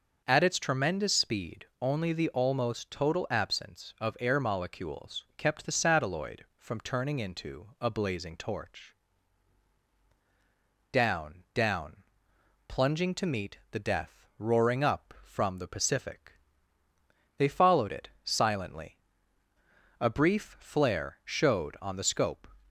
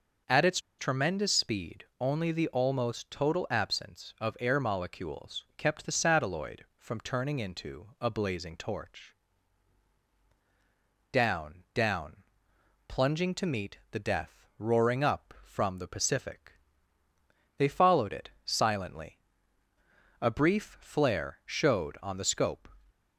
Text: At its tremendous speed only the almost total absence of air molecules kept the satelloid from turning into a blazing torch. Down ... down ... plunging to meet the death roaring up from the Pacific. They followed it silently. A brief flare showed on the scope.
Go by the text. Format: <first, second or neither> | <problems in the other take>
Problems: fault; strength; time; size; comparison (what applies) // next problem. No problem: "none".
first | pauses between "its" and "tremendous"; slight; at 0.5 s; 0.20 s long // pauses between "speed" and "only"; slight; at 1.8 s; 0.16 s long; slight in the first